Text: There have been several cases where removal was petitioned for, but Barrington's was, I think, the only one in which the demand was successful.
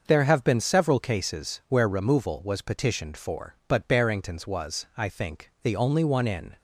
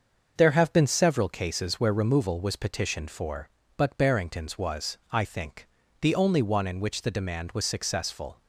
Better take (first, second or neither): second